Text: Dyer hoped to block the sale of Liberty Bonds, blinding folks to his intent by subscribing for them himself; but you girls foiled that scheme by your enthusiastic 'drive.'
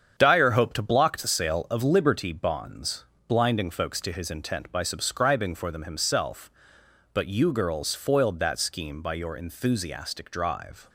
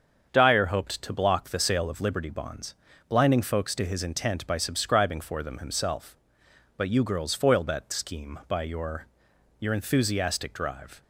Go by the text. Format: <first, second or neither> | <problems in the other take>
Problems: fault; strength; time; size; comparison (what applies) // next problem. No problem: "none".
first | starts louder than the rest; until 1.3 s; 7 dB; strong in the first // says "your" twice; at 9.5 s